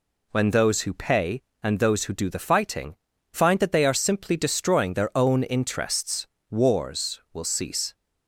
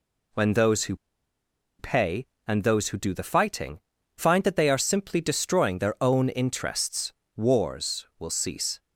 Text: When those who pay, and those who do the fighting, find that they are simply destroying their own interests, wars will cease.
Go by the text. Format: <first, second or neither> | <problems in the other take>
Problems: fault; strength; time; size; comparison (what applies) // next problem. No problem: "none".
first | pauses between "who" and "pay"; noticeable; at 0.9 s; 0.83 s long